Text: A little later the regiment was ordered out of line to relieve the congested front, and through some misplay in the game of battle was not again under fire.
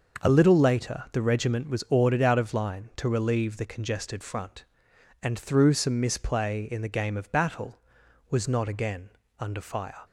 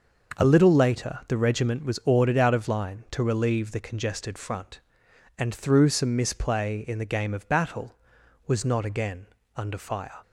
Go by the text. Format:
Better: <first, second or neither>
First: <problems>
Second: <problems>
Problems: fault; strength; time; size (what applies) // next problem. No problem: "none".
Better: neither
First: starts louder than the rest; until 1.3 s; 6 dB // pauses between "again" and "under"; slight; at 9.0 s; 0.30 s long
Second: starts louder than the rest; until 1.4 s; 6 dB // pauses between "again" and "under"; slight; at 9.2 s; 0.30 s long